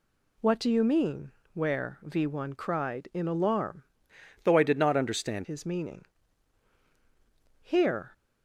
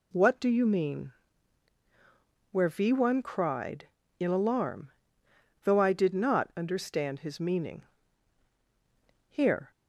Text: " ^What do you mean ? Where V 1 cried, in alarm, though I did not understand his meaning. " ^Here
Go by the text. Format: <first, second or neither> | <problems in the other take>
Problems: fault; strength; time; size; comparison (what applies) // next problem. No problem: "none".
second | changes voice from "though" to "understand"; from 4.4 to 5.4 s; 1.0 s long